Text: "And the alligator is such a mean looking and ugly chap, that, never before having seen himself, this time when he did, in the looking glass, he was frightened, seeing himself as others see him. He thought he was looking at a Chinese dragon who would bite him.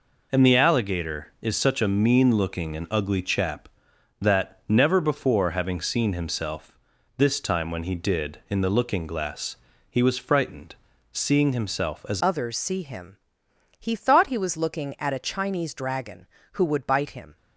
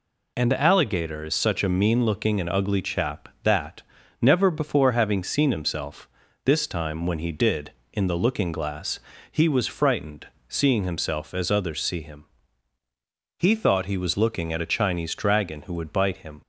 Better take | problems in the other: second | changes voice at "others"; from 12.2 s on; 5.1 s long

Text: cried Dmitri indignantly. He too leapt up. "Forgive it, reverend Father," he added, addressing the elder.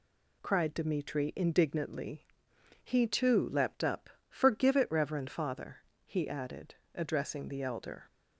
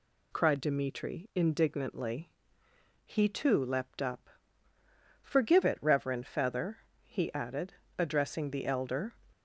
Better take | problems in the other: first | says "Feather" for "Father"; at 6.2 s

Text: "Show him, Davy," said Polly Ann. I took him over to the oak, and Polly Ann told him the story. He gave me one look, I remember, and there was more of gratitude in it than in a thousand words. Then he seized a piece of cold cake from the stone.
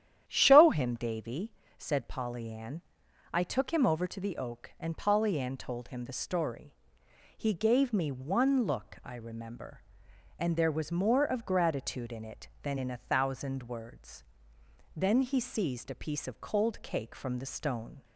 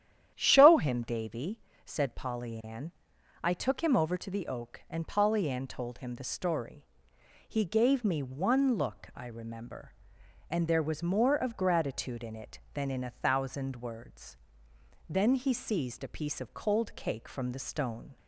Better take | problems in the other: neither | starts louder than the rest; strong; the same in both

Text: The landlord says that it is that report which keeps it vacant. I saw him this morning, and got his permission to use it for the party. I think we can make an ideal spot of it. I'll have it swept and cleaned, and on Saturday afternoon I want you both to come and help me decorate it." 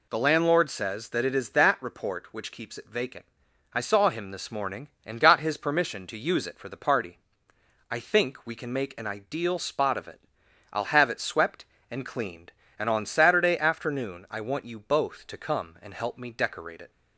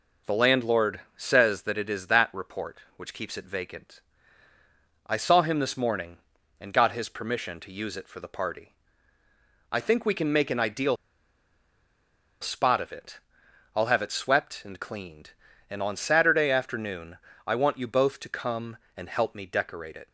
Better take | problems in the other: first | pauses between "landlord" and "says"; slight; at 0.9 s; 0.16 s long // pauses between "ideal" and "spot"; strong; at 10.9 s; 1.4 s long // pauses between "afternoon" and "I"; slight; at 17.1 s; 0.28 s long

